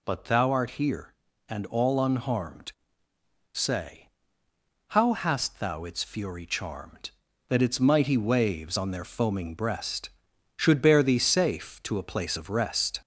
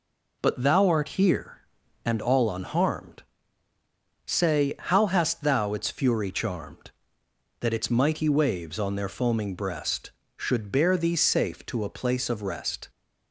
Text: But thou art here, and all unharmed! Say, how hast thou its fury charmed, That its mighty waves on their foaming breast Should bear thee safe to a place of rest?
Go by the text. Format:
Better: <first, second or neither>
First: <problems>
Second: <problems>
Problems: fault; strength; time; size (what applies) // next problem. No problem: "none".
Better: second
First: gets louder; slight; throughout; 2.5 dB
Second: none